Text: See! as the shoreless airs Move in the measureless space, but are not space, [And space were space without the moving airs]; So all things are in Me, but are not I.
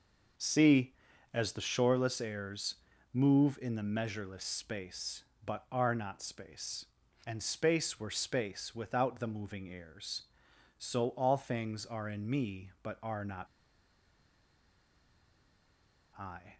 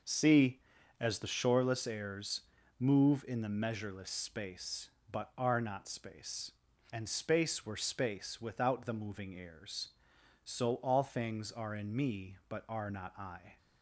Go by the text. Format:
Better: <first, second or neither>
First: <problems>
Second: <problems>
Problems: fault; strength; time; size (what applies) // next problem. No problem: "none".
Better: second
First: pauses between "airs" and "Move"; at 2.7 s; 0.38 s long // pauses between "not" and "I"; strong; at 13.4 s; 2.7 s long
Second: pauses between "airs" and "Move"; at 2.4 s; 0.38 s long